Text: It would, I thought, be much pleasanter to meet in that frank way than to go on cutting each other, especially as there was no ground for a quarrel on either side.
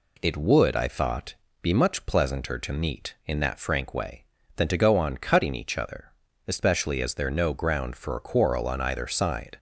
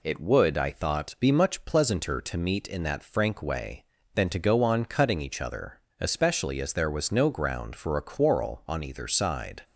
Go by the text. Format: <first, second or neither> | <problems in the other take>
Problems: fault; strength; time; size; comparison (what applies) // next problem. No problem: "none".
second | skips "was"; at 7.2 s